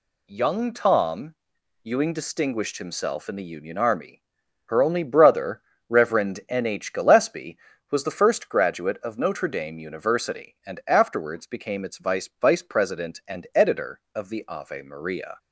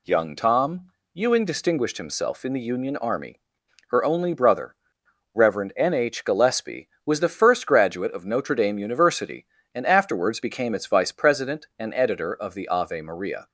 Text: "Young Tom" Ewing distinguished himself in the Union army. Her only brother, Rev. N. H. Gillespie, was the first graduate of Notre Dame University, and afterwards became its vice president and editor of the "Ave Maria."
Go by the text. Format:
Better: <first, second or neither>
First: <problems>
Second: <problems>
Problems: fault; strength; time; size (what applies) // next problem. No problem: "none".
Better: second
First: pauses between "Tom" and "Ewing"; noticeable; at 1.3 s; 0.48 s long // says "vice" twice; at 12.4 s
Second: pauses between "Tom" and "Ewing"; slight; at 0.9 s; 0.22 s long